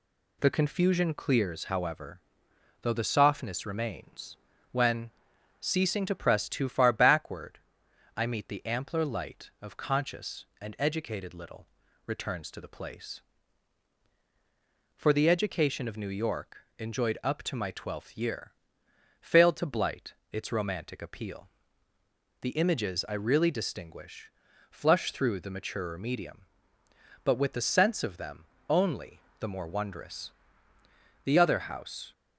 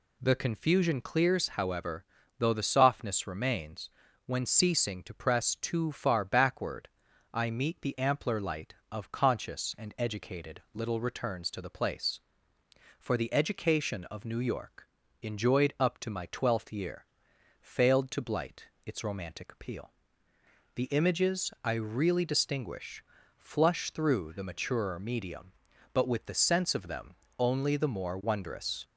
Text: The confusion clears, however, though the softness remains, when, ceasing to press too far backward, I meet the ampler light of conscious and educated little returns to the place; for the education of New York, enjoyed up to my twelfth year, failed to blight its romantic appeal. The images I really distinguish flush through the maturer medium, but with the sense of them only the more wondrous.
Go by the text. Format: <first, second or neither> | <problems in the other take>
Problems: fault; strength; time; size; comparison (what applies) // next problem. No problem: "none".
second | pauses between "little" and "returns"; at 11.6 s; 0.38 s long // pauses between "blight" and "its"; slight; at 20.1 s; 0.18 s long; slight in the second // pauses between "distinguish" and "flush"; at 24.2 s; 0.40 s long; slight in the second // pauses between "them" and "only"; slight; at 28.4 s; 0.26 s long; slight in the second // pauses between "only" and "the"; slight; at 29.1 s; 0.20 s long // goes on to say "The other house"; noticeable; from 31.2 s on; 0.88 s long